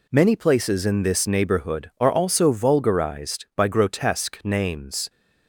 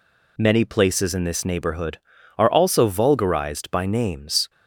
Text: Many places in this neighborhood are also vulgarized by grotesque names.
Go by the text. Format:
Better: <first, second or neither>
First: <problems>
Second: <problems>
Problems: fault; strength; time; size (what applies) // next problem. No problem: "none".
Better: first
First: none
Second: skips "grotesque"; at 3.8 s